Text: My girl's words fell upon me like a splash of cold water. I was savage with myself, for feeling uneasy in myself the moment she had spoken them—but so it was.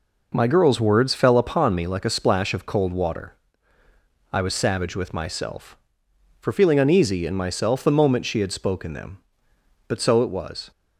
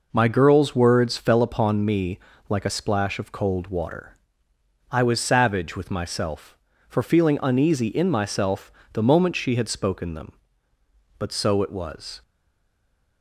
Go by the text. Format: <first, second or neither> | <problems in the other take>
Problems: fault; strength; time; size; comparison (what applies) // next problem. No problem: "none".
first | pauses between "me" and "like"; slight; at 2.1 s; 0.30 s long // pauses between "myself" and "the"; slight; at 8.7 s; 0.21 s long // stays silent after the last word; from 12.2 s on; 1.0 s long